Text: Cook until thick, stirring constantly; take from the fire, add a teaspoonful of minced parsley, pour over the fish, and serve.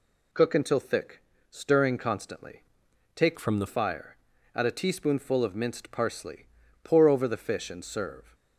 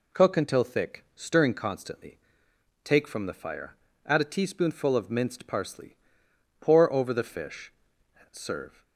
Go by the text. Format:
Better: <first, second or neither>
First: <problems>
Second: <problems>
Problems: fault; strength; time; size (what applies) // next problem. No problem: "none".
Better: second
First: changes voice from "from" to "the"; from 3.3 to 3.6 s; 0.3 s long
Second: none